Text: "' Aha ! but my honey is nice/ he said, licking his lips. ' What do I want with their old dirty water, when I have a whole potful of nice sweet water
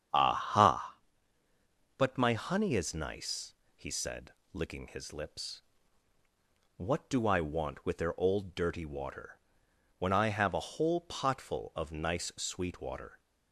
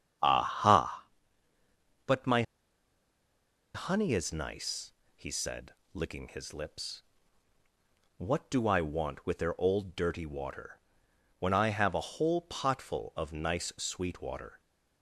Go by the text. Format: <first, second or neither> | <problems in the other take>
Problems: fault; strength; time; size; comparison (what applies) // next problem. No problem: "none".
first | starts louder than the rest; strong; until 2.1 s; 9 dB; strong in the first // pauses between "my" and "honey"; strong; at 2.4 s; 1.3 s long